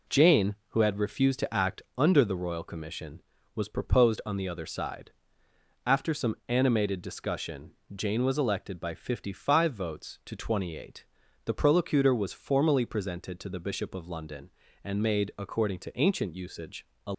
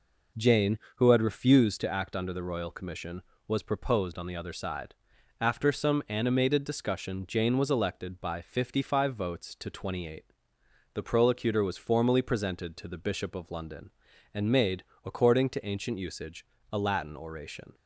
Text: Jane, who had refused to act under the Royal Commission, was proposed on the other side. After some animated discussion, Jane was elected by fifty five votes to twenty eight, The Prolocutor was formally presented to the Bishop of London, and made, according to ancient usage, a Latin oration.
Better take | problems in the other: second | pauses between "act" and "under"; slight; at 1.8 s; 0.16 s long // stops before "Latin oration"; at 17.1 s

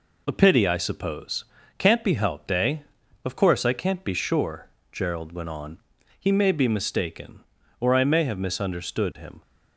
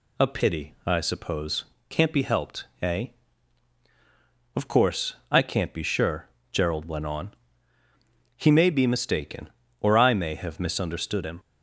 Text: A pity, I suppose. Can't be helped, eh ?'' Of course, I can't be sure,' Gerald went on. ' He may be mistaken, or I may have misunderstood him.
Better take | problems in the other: second | gets quieter; slight; throughout; 3 dB

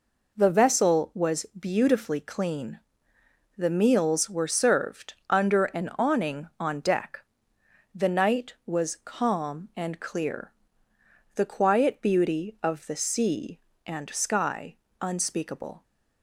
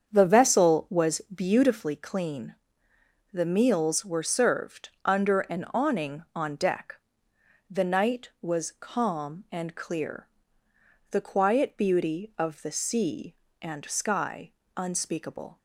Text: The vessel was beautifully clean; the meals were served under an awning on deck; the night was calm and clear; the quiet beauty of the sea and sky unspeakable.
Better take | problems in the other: first | starts louder than the rest; strong; until 1.7 s; 7.5 dB // pauses between "served" and "under"; slight; at 4.8 s; 0.16 s long; slight in the first // pauses between "sky" and "unspeakable"; slight; at 14.5 s; 0.26 s long; slight in the first

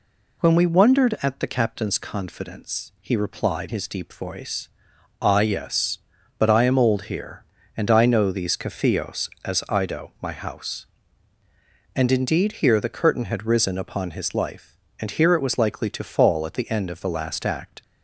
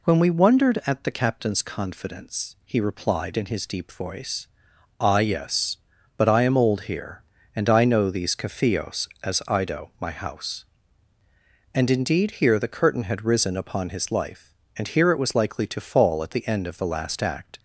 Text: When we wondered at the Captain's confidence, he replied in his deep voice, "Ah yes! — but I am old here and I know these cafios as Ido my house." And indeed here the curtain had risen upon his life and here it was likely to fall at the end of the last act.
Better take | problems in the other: second | skips "in"; at 3.6 s

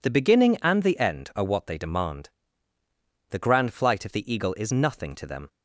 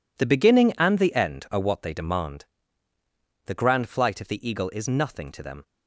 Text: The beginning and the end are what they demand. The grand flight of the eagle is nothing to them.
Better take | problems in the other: first | gets quieter; strong; throughout; 12.5 dB

